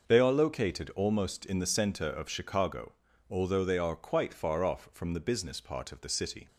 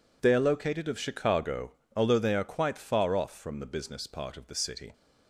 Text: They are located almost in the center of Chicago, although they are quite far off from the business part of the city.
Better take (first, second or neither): first